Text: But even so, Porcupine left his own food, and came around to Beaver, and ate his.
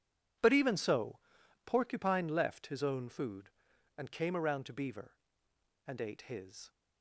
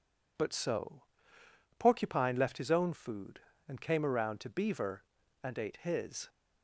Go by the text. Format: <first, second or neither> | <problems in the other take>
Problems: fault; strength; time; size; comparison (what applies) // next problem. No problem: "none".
first | skips "even"; at 0.5 s